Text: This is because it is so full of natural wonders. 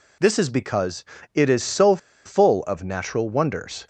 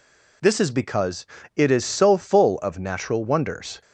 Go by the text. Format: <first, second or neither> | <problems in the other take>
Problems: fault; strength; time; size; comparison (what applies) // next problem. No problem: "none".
second | pauses between "because" and "it"; slight; at 1.0 s; 0.30 s long; slight in the second // pauses between "so" and "full"; slight; at 1.9 s; 0.28 s long